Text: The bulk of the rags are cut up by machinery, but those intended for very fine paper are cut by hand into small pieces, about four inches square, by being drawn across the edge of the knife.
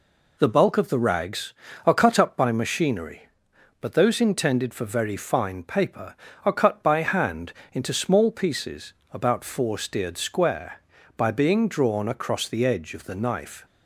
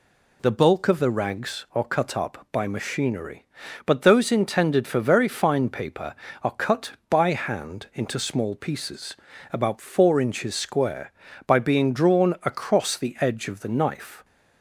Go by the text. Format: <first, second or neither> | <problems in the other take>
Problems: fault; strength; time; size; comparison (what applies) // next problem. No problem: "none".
second | pauses between "hand" and "into"; slight; at 7.5 s; 0.18 s long // says "steered" for "inches"; at 9.7 s